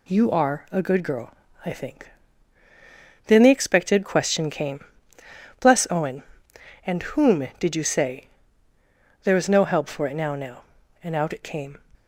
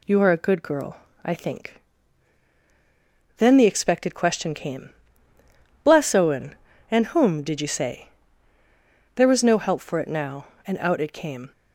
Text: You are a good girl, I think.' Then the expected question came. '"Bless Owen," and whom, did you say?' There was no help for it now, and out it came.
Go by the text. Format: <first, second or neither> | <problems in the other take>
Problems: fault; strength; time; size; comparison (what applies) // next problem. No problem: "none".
second | says "now" twice; at 10.3 s